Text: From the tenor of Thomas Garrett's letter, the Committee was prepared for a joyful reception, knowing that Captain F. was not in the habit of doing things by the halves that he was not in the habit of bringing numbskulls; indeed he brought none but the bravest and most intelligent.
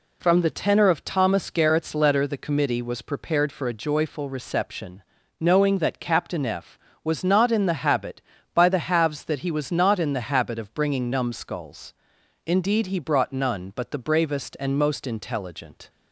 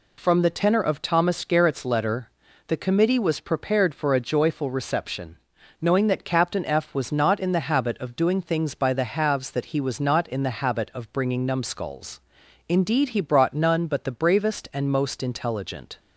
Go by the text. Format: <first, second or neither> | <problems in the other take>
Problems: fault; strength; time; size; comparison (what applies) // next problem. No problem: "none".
second | skips "of doing things"; at 8.3 s